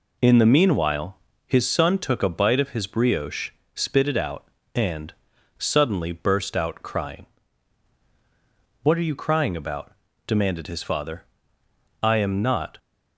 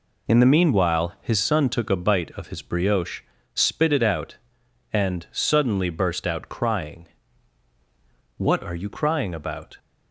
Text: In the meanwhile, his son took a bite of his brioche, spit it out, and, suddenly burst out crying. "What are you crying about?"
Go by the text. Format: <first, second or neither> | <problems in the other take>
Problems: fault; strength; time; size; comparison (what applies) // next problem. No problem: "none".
second | goes on to say "demanded his father I am not"; strong; from 10.2 s on; 2.5 s long